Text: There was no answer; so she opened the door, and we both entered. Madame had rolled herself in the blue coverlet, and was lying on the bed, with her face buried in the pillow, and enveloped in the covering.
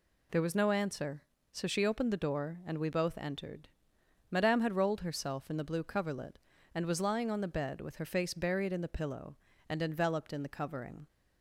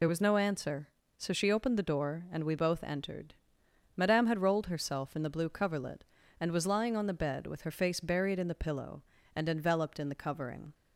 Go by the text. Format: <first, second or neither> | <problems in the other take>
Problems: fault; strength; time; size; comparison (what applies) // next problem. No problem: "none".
first | loses the start of "There"; at 0.0 s; 40 ms